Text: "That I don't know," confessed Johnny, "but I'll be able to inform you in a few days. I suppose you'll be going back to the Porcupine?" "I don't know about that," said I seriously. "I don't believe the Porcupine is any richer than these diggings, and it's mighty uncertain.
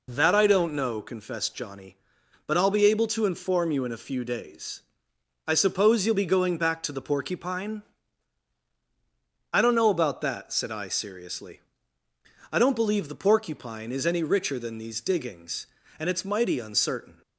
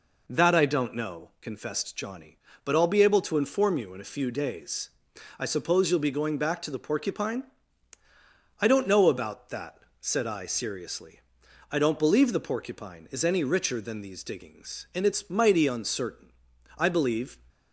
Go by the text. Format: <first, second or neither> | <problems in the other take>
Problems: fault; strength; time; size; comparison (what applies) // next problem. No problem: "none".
first | goes on to say "I believe"; noticeable; from 16.7 s on; 0.62 s long